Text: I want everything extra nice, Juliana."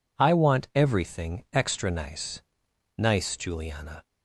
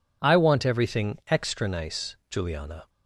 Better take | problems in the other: second | says "nice" twice; at 2.9 s

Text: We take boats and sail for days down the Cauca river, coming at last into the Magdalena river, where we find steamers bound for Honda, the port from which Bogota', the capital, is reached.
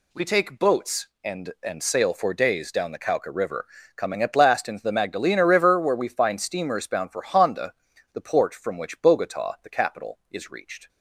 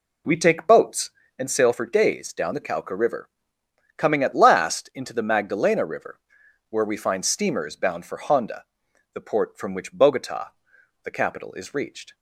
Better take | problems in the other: second | says "and" twice; at 1.6 s

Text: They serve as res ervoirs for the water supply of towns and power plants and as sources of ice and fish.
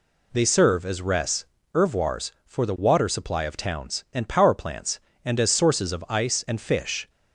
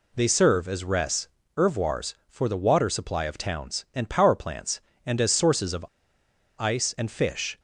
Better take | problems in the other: first | pauses between "res" and "ervoirs"; slight; at 1.2 s; 0.30 s long; slight in the first // pauses between "of" and "ice"; noticeable; at 5.8 s; 0.71 s long

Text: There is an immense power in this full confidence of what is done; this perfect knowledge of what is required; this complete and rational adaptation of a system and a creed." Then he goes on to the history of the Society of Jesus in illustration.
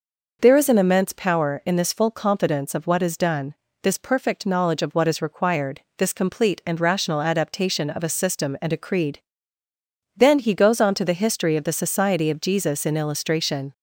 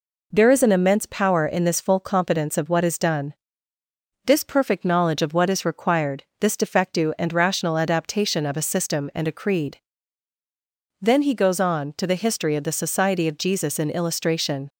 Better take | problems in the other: first | says "defectu" for "complete"; at 6.5 s

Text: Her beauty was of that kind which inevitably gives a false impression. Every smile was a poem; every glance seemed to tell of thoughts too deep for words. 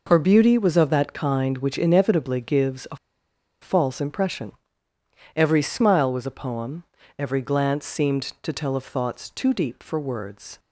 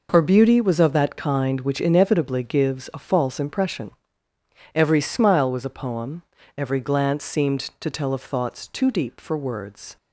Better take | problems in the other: second | pauses between "a" and "false"; noticeable; at 2.9 s; 0.66 s long

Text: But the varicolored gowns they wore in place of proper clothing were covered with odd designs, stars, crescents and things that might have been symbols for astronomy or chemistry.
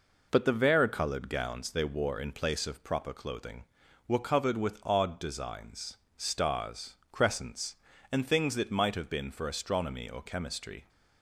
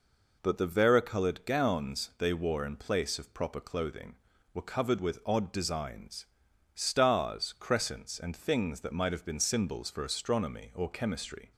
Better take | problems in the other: second | skips "symbols"; at 9.3 s

